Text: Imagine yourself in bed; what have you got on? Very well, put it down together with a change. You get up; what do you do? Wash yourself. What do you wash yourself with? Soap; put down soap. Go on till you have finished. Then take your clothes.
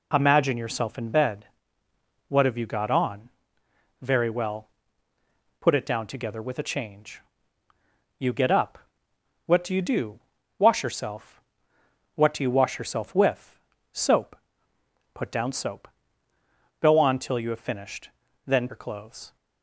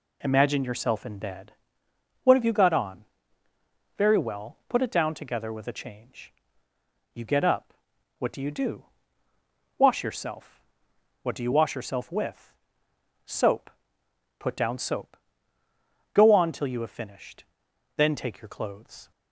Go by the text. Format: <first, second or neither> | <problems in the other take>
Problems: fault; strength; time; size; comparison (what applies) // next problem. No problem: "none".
second | skips "take"; at 18.6 s